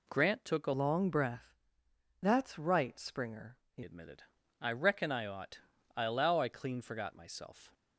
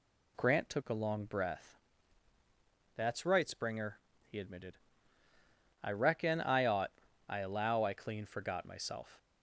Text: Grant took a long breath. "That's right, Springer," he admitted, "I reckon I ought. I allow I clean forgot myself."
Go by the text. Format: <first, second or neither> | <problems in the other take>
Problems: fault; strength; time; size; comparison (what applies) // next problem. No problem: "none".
second | changes voice from "long" to "he"; from 0.7 to 3.8 s; 3.1 s long